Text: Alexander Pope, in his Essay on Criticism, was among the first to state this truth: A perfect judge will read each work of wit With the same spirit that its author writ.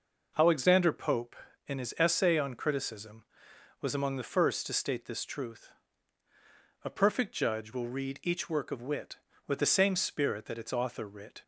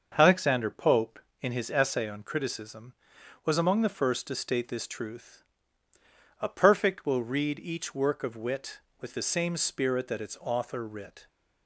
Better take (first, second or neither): first